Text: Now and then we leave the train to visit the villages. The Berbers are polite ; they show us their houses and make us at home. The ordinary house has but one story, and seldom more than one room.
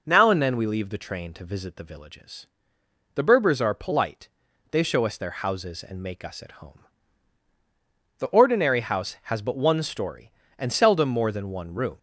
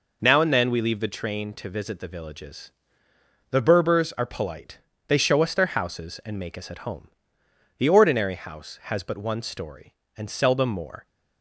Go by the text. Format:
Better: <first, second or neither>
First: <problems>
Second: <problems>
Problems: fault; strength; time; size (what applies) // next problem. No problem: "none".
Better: first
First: none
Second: stops before "than one room"; at 11.0 s